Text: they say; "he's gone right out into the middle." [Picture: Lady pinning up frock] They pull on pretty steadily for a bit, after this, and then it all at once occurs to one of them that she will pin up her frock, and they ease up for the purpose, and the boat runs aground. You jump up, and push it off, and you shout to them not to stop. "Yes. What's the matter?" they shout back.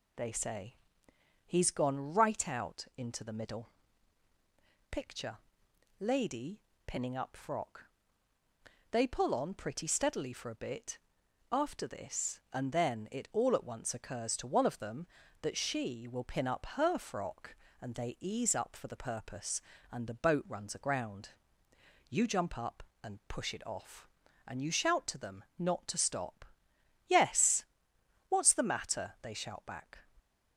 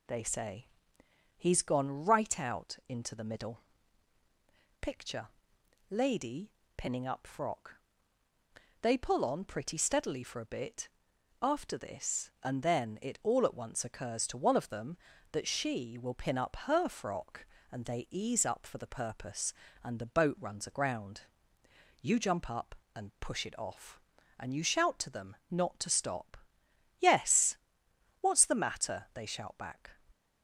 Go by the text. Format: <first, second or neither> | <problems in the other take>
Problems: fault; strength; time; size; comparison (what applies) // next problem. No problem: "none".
neither | pauses between "Lady" and "pinning"; slight; the same in both // pauses between "frock" and "They"; the same in both